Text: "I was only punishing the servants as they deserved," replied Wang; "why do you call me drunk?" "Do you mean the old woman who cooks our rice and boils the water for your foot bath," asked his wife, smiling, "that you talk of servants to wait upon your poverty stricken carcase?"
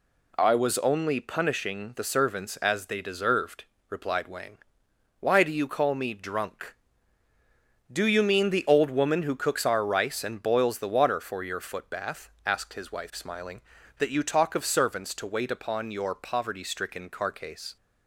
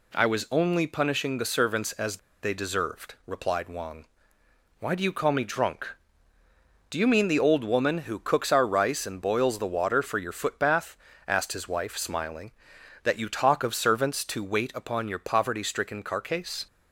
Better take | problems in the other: first | pauses between "as" and "they"; slight; at 2.1 s; 0.24 s long

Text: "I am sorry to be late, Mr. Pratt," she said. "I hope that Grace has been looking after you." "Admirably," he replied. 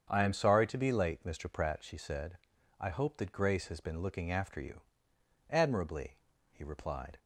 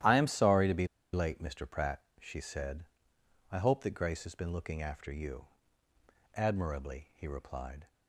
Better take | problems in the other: first | starts louder than the rest; strong; until 1.3 s; 12.5 dB; strong in the first // pauses between "be" and "late"; slight; at 0.8 s; 0.26 s long

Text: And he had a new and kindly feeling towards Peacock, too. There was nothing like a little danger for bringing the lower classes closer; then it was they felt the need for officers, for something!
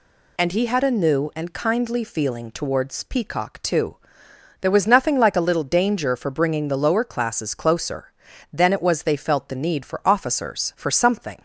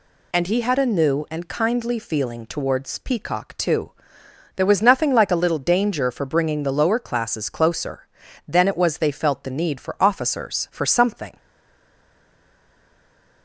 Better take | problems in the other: first | stays silent after the last word; noticeable; from 11.3 s on; 2.1 s long

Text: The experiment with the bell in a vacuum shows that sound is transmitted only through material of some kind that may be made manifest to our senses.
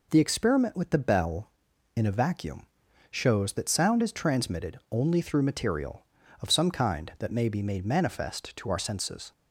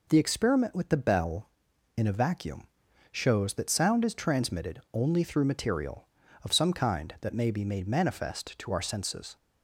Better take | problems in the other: neither | pauses between "vacuum" and "shows"; noticeable; the same in both

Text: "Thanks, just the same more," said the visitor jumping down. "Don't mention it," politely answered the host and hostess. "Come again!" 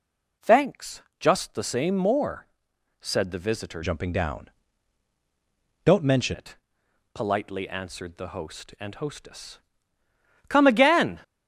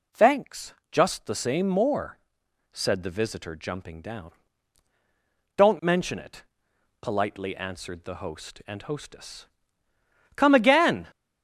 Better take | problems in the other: second | changes voice from "jumping" to "mention"; from 3.8 to 6.3 s; 2.5 s long

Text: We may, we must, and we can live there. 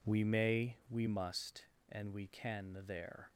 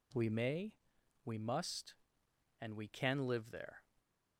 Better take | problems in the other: second | skips "live"; at 2.8 s

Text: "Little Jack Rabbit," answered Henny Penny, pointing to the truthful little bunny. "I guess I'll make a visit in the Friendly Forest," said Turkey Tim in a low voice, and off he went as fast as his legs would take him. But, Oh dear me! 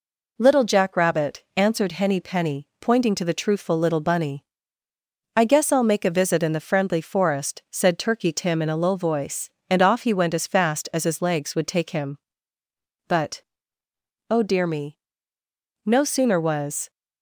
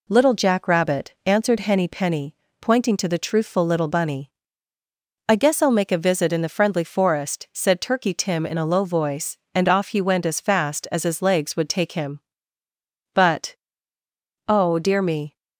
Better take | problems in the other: second | goes on to say "No sooner was"; noticeable; from 15.8 s on; 1.0 s long

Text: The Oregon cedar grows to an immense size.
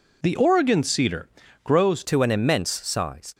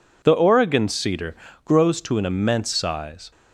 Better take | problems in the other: second | pauses between "cedar" and "grows"; slight; at 1.2 s; 0.34 s long; slight in the second // changes voice at "to"; from 2.0 s on; 1.3 s long

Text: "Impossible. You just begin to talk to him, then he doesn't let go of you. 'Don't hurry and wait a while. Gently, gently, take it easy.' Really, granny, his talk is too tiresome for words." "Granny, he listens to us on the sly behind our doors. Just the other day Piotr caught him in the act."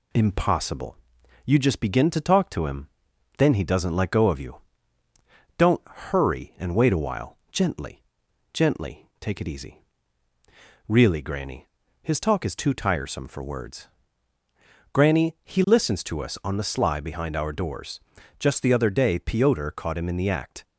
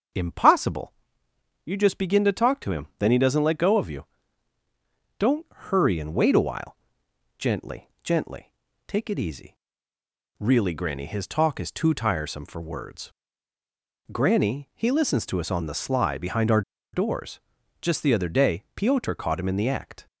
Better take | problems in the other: first | starts louder than the rest; until 1.8 s; 6.5 dB // pauses between "our" and "doors"; slight; at 16.6 s; 0.32 s long

